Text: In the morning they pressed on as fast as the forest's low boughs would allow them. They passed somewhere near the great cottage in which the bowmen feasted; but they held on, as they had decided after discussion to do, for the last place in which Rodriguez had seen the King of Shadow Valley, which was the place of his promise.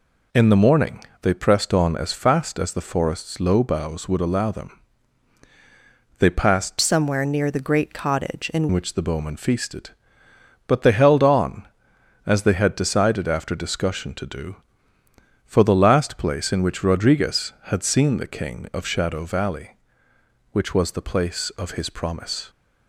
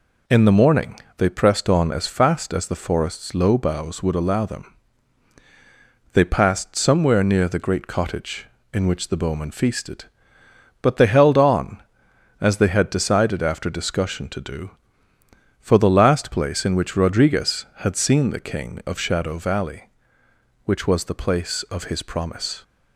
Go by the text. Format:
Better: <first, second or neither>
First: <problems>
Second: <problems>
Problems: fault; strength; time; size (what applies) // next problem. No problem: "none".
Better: second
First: pauses between "morning" and "they"; slight; at 1.0 s; 0.20 s long // changes voice from "somewhere" to "in"; from 6.7 to 8.6 s; 1.9 s long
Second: pauses between "morning" and "they"; slight; at 0.9 s; 0.20 s long